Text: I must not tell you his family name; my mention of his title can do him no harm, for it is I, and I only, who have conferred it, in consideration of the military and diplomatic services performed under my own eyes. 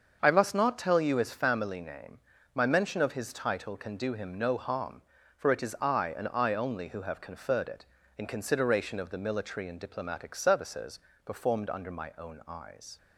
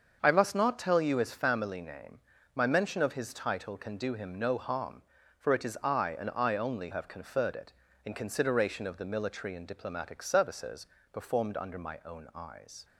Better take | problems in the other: first | starts louder than the rest; until 1.2 s; 7 dB; also in the first // skips "who"; at 6.9 s // pauses between "services" and "performed"; slight; at 10.8 s; 0.26 s long; slight in the first

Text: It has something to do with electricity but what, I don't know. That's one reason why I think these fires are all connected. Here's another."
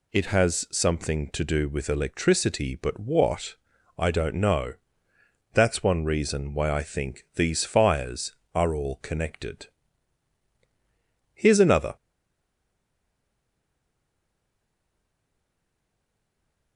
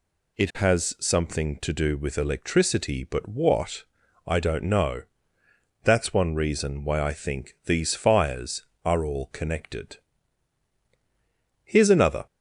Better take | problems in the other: second | stays silent after the last word; strong; from 11.9 s on; 4.8 s long

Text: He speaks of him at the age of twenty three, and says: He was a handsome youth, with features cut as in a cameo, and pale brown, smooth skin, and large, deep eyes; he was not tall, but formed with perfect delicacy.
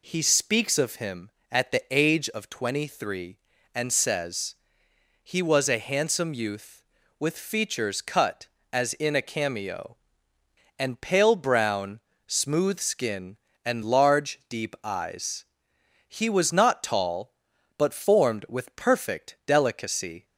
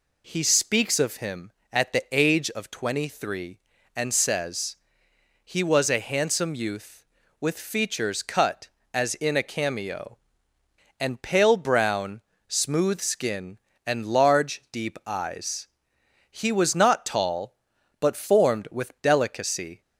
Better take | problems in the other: first | skips "perfect"; at 18.9 s

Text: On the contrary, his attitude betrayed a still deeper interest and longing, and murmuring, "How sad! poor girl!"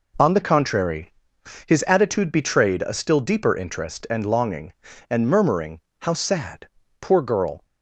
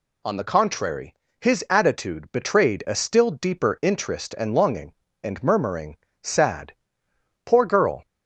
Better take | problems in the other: first | skips "How"; at 6.0 s

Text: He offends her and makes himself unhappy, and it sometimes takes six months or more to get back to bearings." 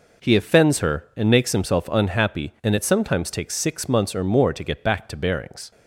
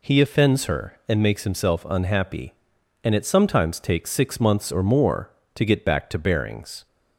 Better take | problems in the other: neither | none

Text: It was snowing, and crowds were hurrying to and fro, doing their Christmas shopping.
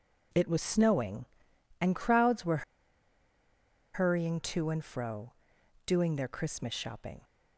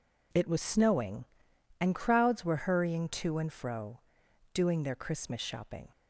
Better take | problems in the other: second | pauses between "were" and "hurrying"; strong; at 2.6 s; 1.3 s long

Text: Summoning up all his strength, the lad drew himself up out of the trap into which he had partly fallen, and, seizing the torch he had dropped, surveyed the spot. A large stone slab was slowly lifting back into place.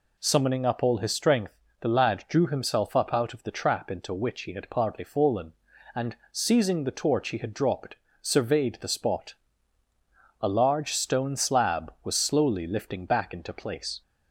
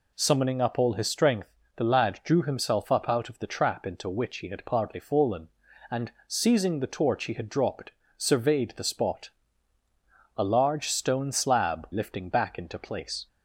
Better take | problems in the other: first | skips "was slowly"; at 11.9 s

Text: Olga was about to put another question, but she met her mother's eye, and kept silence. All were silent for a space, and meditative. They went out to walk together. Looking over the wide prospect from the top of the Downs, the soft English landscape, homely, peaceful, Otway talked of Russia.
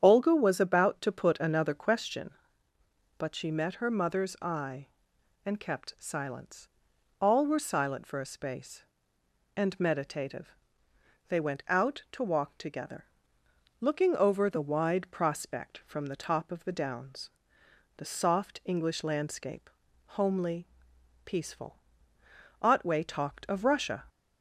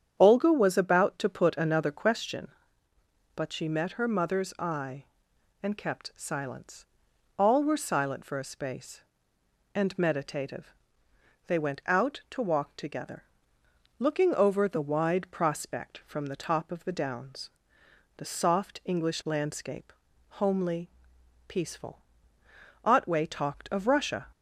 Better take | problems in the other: neither | starts louder than the rest; strong; the same in both

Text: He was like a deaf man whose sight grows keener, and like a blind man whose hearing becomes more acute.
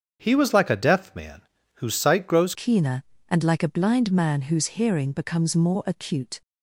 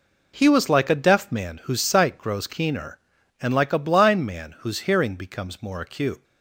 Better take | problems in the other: second | starts louder than the rest; strong; until 1.2 s; 7 dB // pauses between "man" and "whose"; slight; at 1.4 s; 0.36 s long // changes voice at "keener"; from 2.5 s on; 3.9 s long

